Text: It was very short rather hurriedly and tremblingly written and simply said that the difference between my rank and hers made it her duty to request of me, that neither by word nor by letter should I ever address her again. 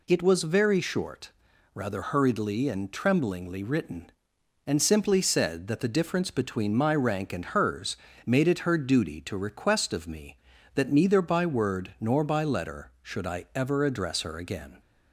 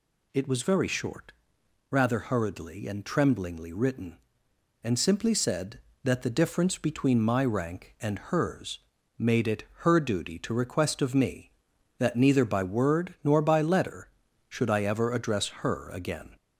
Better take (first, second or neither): first